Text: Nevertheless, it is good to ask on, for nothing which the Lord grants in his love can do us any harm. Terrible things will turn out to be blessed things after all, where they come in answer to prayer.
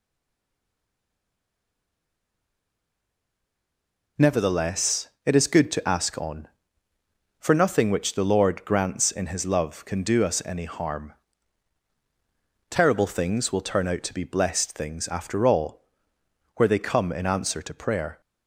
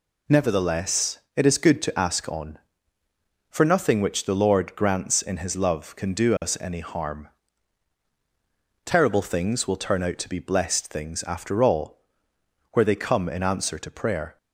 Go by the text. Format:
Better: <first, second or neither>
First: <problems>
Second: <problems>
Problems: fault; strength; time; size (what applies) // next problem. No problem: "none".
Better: second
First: stays silent before the first word; strong; until 4.1 s; 4.1 s long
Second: none